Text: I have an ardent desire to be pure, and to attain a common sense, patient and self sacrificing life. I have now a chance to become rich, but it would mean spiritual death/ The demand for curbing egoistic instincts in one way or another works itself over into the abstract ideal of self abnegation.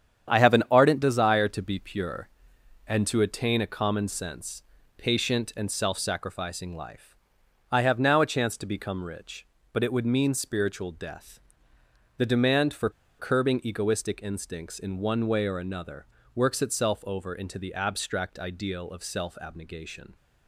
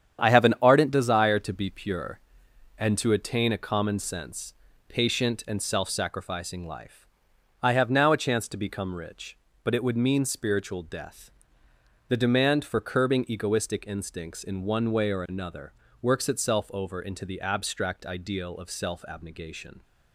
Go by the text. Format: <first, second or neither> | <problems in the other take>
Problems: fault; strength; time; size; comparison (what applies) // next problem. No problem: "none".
second | starts louder than the rest; strong; until 1.3 s; 8.5 dB; strong in the second // pauses between "for" and "curbing"; slight; at 12.9 s; 0.28 s long // pauses between "another" and "works"; slight; at 16.0 s; 0.28 s long; slight in the second